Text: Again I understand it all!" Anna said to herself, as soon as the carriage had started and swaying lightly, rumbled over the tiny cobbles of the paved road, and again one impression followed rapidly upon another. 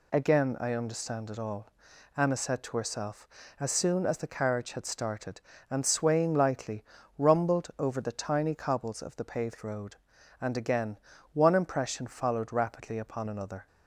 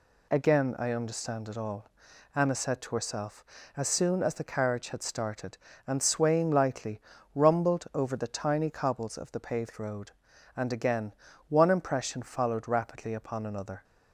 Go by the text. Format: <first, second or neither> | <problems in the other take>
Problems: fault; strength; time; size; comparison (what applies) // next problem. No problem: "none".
neither | pauses between "again" and "one"; slight; the same in both